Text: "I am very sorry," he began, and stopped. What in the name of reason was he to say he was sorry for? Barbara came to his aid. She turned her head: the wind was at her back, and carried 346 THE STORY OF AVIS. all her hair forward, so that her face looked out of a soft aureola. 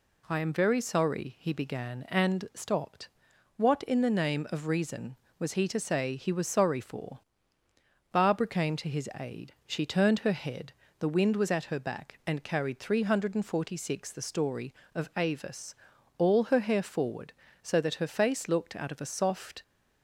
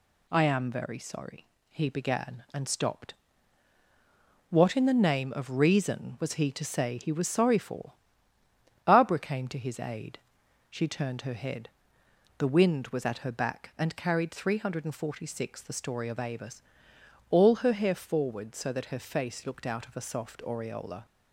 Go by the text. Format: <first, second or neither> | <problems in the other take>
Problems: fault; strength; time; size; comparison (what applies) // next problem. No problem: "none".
second | stops before "aureola"; at 19.6 s